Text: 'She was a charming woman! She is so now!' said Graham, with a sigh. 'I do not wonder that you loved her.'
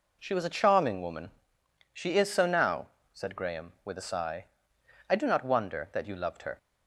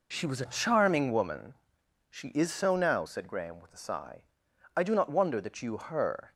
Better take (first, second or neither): first